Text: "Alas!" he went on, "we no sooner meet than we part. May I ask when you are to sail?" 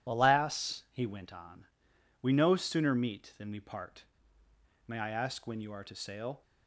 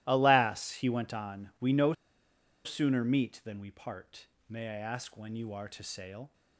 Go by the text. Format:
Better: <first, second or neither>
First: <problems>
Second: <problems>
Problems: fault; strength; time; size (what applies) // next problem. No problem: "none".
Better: first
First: none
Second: starts louder than the rest; strong; until 1.0 s; 16 dB // pauses between "no" and "sooner"; noticeable; at 1.9 s; 0.70 s long